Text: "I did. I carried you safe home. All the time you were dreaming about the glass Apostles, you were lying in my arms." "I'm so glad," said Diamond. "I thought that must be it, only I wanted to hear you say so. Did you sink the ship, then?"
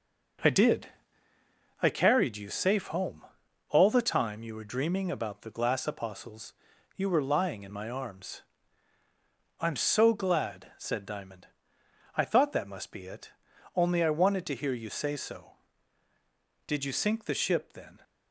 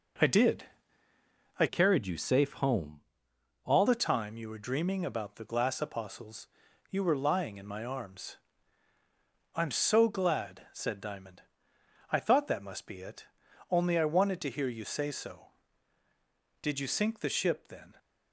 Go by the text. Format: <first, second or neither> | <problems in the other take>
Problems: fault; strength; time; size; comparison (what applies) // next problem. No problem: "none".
first | changes voice from "carried" to "All"; from 1.6 to 3.8 s; 2.2 s long